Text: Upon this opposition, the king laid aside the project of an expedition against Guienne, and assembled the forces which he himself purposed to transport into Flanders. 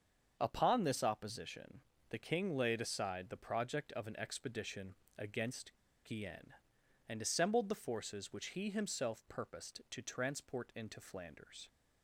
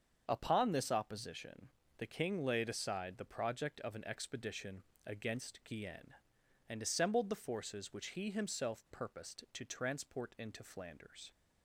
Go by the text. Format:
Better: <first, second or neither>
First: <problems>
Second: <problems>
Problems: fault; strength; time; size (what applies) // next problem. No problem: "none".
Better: second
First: starts louder than the rest; until 1.4 s; 7 dB // pauses between "expedition" and "against"; slight; at 4.9 s; 0.20 s long // pauses between "against" and "Guienne"; slight; at 5.7 s; 0.31 s long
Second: starts louder than the rest; until 1.2 s; 7 dB // pauses between "expedition" and "against"; slight; at 4.8 s; 0.20 s long